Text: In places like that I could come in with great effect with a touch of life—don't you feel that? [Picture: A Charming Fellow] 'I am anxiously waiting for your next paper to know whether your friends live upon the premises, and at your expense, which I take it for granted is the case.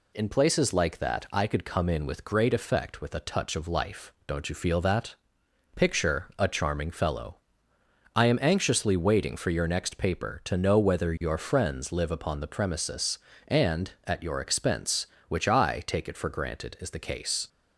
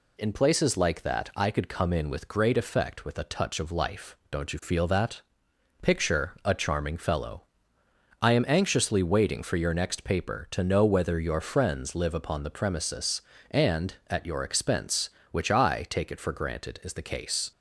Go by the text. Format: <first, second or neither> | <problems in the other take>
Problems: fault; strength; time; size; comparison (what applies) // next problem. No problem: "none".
neither | pauses between "Fellow" and "I"; noticeable; the same in both